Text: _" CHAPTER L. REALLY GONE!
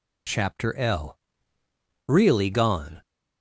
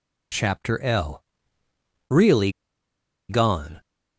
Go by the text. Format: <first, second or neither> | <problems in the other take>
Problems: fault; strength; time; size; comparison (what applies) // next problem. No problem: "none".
first | pauses between "REALLY" and "GONE"; noticeable; at 2.5 s; 0.78 s long